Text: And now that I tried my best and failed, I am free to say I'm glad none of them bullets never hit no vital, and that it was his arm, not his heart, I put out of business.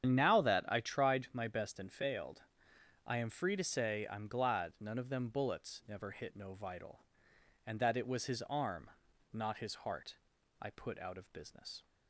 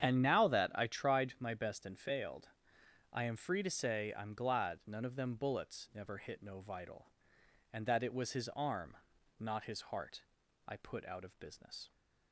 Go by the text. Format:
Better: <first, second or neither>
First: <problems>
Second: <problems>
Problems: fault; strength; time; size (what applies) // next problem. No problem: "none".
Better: second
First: loses the start of "And"; at 0.0 s; 100 ms // starts louder than the rest; strong; until 1.0 s; 8.5 dB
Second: starts louder than the rest; strong; until 1.0 s; 8.5 dB